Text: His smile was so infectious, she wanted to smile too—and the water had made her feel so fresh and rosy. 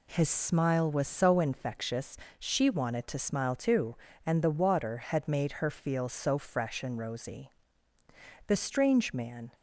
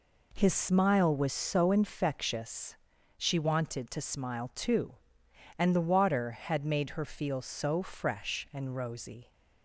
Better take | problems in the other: second | goes on to say "The strange man"; noticeable; from 8.4 s on; 1.0 s long

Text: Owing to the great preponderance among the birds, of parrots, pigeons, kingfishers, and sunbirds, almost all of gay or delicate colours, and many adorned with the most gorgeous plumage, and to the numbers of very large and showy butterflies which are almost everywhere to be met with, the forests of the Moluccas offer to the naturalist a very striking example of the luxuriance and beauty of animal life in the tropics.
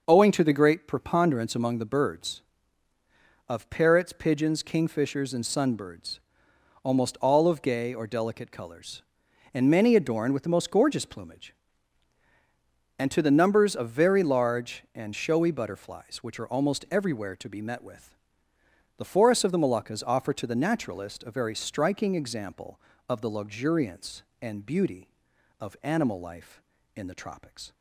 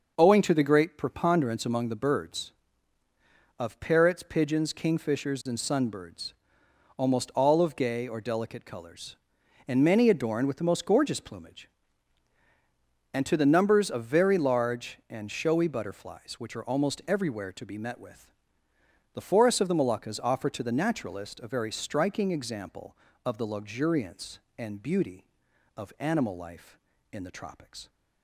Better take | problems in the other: neither | none

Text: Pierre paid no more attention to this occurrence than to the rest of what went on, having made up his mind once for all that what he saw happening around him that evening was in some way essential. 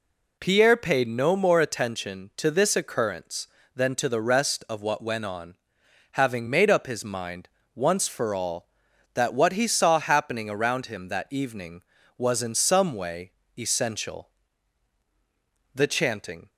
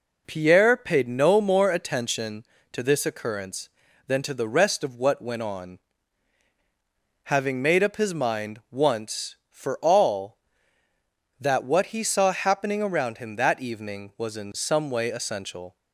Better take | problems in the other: second | pauses between "mind" and "once"; slight; at 7.4 s; 0.26 s long // pauses between "way" and "essential"; slight; at 13.3 s; 0.26 s long // goes on to say "The chanting"; noticeable; from 15.7 s on; 0.76 s long

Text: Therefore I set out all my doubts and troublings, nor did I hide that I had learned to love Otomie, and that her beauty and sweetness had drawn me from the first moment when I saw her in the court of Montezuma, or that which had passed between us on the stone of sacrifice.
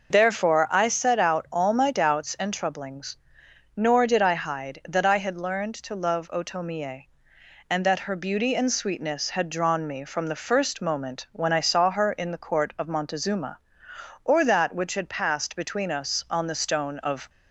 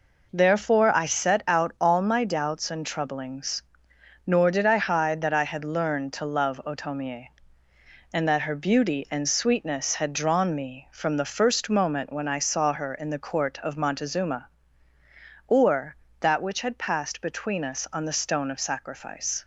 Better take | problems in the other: second | stops before "sacrifice"; at 17.2 s

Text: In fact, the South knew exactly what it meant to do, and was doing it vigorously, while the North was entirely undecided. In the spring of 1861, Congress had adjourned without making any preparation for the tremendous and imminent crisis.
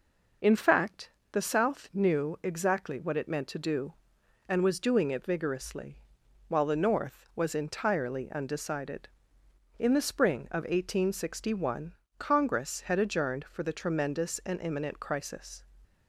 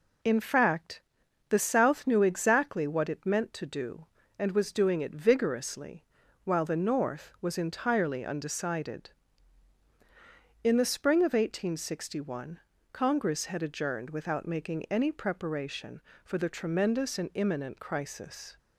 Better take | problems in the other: second | skips "without making any preparation"; at 13.4 s

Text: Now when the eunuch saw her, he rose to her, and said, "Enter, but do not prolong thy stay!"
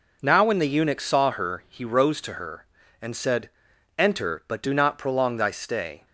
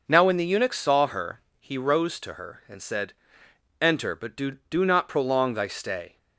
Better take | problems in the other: first | says "do" twice; at 4.6 s

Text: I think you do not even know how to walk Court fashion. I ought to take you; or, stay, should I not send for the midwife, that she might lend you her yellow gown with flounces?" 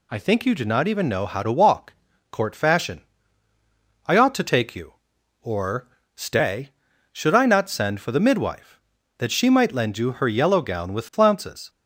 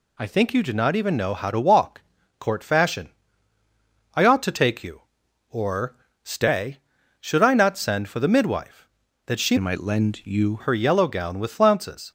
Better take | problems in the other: first | pauses between "walk" and "Court"; at 2.0 s; 0.38 s long; also in the first // changes voice from "might" to "you"; from 9.5 to 10.6 s; 1.1 s long

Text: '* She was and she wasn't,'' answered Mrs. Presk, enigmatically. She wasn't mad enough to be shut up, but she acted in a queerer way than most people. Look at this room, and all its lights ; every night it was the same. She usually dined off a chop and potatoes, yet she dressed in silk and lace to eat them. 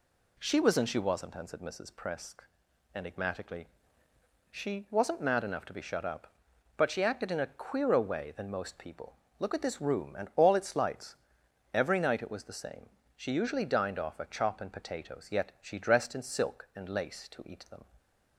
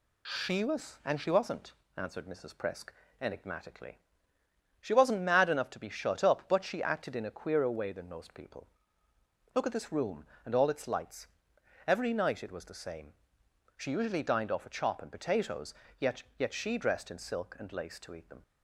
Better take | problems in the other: first | says "yet" twice; at 16.4 s

